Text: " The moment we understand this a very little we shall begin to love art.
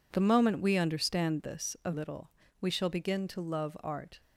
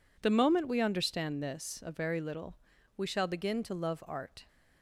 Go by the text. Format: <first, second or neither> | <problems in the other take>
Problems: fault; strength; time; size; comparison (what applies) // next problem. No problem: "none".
second | skips "very"; at 1.9 s // pauses between "little" and "we"; slight; at 2.3 s; 0.32 s long; also in the second